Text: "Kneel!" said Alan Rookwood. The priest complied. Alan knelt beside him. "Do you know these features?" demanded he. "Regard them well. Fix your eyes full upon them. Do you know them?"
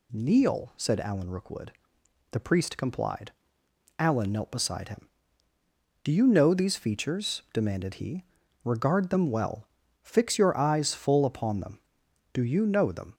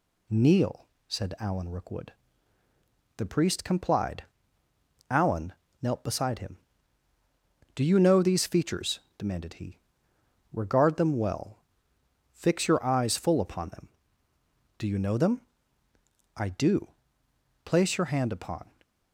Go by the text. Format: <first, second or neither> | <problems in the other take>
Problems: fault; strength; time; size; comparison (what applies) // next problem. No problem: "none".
first | pauses between "Alan" and "knelt"; slight; at 5.5 s; 0.30 s long // goes on to say "I do Place your hand upon"; strong; from 16.3 s on; 2.3 s long